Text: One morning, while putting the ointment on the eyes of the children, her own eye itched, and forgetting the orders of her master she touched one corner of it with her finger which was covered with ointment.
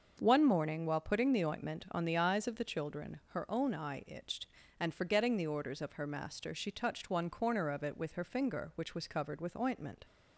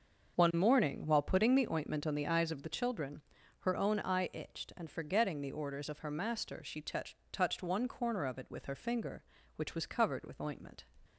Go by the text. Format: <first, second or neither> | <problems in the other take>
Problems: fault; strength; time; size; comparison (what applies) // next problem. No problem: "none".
first | starts louder than the rest; until 1.4 s; 6.5 dB; also in the first // says "touched" twice; at 7.3 s